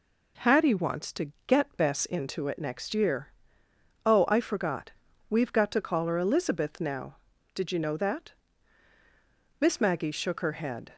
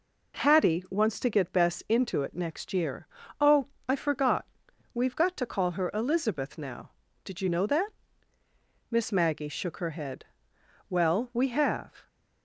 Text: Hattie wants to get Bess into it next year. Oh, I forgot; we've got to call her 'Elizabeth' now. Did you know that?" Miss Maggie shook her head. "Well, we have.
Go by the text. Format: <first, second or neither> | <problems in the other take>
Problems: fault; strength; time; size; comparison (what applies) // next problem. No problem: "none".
second | stops before "Well we have"; at 10.9 s